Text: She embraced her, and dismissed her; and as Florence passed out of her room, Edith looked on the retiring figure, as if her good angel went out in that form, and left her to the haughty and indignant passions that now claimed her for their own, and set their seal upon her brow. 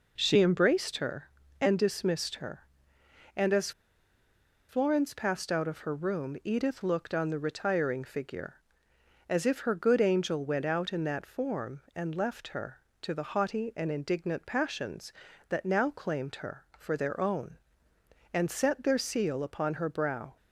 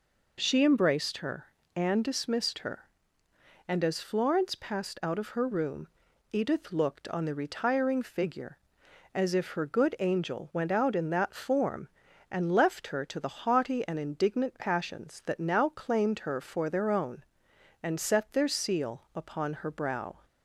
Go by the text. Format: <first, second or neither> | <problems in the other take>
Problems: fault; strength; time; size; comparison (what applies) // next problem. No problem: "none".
second | pauses between "as" and "Florence"; at 3.7 s; 0.98 s long